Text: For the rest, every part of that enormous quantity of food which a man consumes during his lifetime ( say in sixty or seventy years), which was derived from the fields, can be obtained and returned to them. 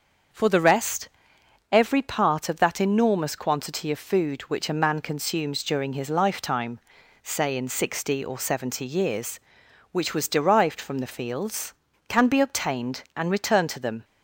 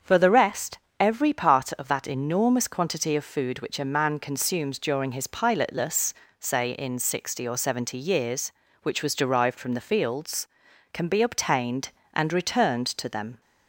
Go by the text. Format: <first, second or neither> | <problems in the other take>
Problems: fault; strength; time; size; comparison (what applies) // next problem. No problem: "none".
first | starts louder than the rest; strong; until 1.2 s; 7 dB; also in the first // says "pilotless" for "lifetime"; at 5.2 s